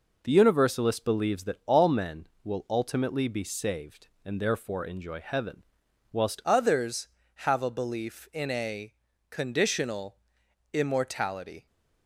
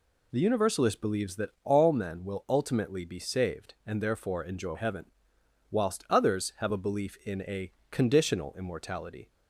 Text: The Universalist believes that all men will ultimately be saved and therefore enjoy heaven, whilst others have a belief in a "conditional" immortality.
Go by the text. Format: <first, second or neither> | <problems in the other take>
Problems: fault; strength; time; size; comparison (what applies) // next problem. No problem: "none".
second | changes voice at "others"; from 6.4 s on; 5.2 s long // pauses between "a" and "conditional"; at 8.9 s; 0.38 s long; slight in the second // pauses between "conditional" and "immortality"; noticeable; at 10.1 s; 0.54 s long